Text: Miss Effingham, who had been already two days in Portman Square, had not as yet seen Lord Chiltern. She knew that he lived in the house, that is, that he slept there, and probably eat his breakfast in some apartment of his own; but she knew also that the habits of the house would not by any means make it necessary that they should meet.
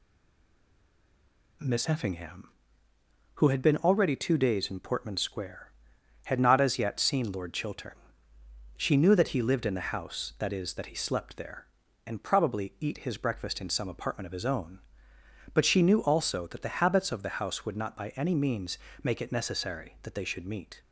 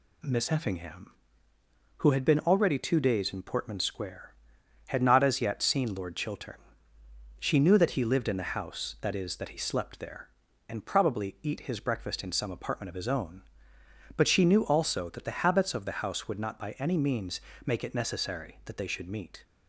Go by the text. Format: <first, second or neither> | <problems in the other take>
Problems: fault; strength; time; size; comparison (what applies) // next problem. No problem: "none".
second | stays silent before the first word; noticeable; until 1.6 s; 1.6 s long // pauses between "means" and "make"; slight; at 18.7 s; 0.24 s long; slight in the second